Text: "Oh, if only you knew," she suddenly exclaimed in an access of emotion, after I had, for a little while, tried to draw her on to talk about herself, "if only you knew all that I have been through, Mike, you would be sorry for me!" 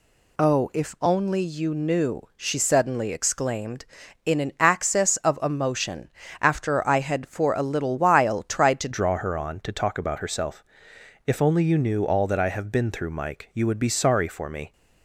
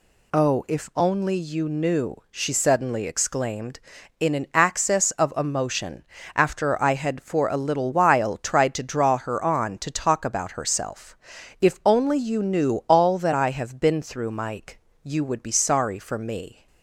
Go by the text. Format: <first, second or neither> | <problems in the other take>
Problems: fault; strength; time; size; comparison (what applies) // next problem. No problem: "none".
second | changes voice at "draw"; from 8.9 s on; 5.8 s long